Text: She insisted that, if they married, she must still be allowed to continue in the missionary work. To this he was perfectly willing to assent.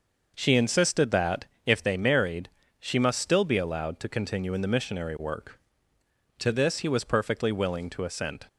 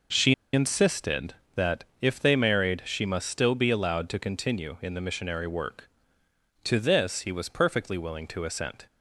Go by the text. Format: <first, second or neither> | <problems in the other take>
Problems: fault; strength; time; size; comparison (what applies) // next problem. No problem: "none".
first | pauses between "She" and "insisted"; slight; at 0.3 s; 0.20 s long